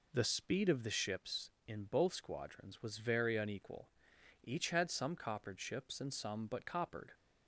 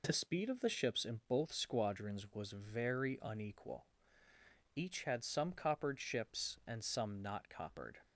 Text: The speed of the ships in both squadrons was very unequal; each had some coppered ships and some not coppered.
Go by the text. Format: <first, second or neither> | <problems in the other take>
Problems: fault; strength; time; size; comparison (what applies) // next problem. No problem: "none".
second | says "but" for "not"; at 6.4 s